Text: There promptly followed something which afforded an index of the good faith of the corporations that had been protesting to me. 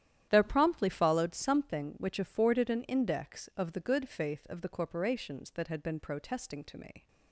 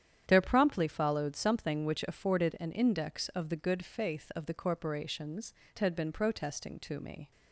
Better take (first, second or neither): first